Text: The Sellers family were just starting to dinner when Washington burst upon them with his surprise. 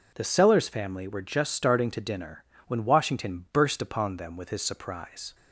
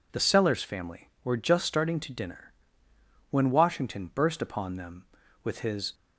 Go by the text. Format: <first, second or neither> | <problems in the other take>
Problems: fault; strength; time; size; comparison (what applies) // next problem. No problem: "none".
first | pauses between "dinner" and "when"; noticeable; at 2.5 s; 0.78 s long; slight in the first // stops before "surprise"; at 5.9 s